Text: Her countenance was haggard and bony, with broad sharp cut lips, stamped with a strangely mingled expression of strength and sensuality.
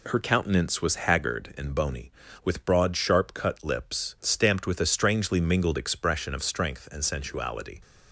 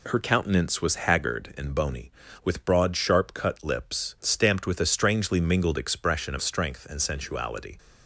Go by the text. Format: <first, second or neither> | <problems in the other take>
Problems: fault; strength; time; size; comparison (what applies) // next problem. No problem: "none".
neither | none